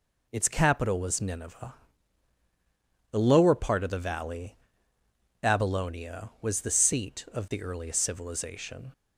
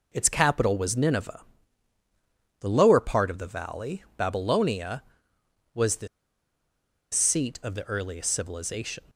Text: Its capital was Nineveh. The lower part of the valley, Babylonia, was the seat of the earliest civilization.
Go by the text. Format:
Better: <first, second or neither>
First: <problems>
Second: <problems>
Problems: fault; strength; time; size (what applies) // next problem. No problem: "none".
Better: first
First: none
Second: pauses between "the" and "seat"; at 6.0 s; 1.0 s long